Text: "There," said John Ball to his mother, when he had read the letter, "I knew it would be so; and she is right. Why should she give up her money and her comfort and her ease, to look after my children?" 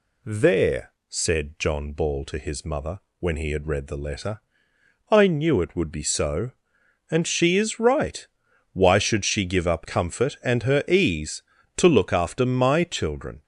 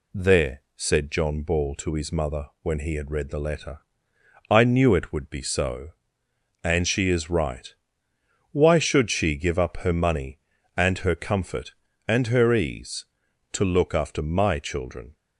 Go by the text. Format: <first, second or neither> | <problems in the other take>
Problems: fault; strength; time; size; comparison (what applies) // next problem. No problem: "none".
second | skips "her money and her"; at 9.8 s